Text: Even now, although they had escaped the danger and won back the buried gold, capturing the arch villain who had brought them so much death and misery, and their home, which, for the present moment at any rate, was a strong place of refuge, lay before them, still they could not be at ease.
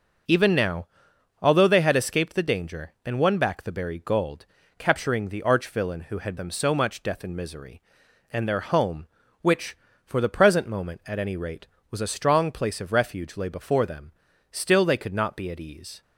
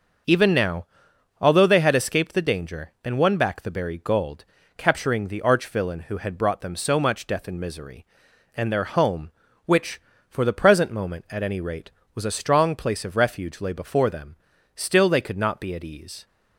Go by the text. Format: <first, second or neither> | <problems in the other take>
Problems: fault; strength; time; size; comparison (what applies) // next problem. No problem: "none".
second | starts louder than the rest; until 1.8 s; 6.5 dB; also in the second // skips "brought"; at 6.3 s